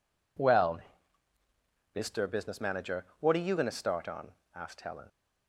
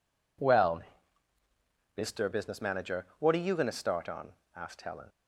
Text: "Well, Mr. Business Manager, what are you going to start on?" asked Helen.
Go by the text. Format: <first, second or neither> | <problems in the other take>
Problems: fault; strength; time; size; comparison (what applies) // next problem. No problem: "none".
neither | none